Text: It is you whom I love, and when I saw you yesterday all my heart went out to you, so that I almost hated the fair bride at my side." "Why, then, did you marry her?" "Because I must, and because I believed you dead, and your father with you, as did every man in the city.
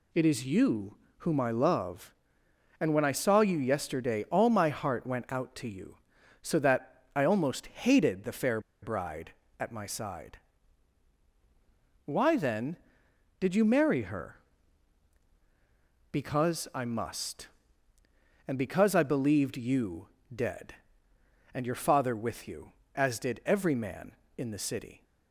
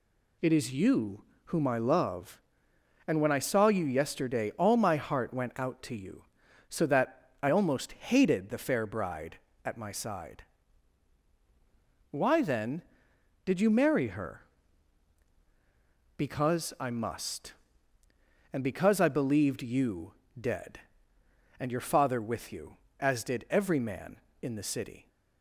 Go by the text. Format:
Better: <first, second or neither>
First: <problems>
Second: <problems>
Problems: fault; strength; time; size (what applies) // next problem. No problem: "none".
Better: second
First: pauses between "you" and "whom"; slight; at 0.9 s; 0.24 s long // pauses between "fair" and "bride"; slight; at 8.5 s; 0.23 s long // pauses between "you" and "dead"; slight; at 20.0 s; 0.26 s long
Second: pauses between "you" and "whom"; slight; at 1.2 s; 0.24 s long // pauses between "you" and "dead"; slight; at 20.1 s; 0.26 s long